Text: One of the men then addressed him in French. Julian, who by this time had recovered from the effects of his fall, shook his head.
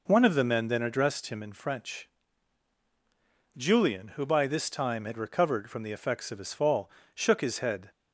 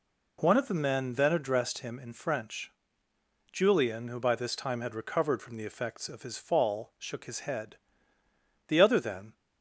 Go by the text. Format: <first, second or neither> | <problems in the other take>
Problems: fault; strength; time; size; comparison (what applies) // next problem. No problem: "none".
first | goes on to say "The other then"; noticeable; from 8.6 s on; 0.66 s long